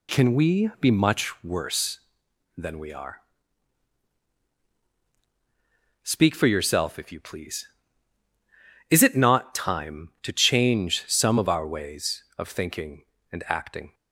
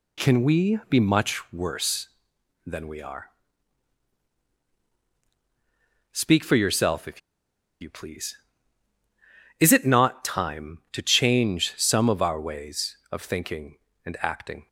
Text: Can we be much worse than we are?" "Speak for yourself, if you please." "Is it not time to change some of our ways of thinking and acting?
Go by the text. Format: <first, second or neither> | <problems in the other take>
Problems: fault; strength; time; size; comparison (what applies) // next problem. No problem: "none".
first | pauses between "if" and "you"; noticeable; at 7.2 s; 0.61 s long